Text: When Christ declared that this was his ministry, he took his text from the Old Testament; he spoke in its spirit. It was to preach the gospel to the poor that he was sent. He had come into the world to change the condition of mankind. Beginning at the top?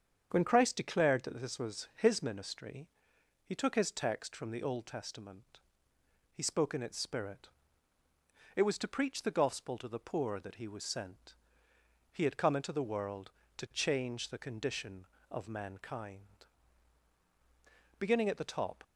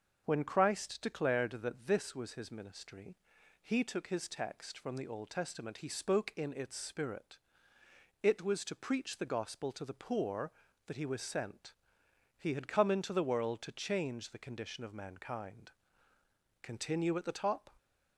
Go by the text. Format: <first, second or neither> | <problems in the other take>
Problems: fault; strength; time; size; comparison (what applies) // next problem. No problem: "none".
first | starts louder than the rest; until 1.2 s; 6.5 dB; strong in the first // says "Continue" for "Beginning"; at 16.6 s